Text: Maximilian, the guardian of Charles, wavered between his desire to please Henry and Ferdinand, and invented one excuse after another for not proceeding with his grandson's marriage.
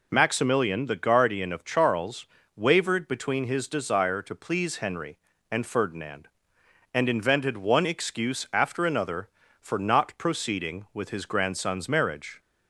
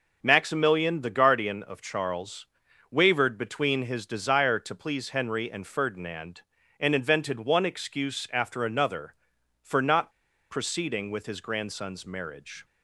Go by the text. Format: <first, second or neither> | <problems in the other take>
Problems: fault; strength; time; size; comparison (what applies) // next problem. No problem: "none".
first | pauses between "not" and "proceeding"; at 10.1 s; 0.38 s long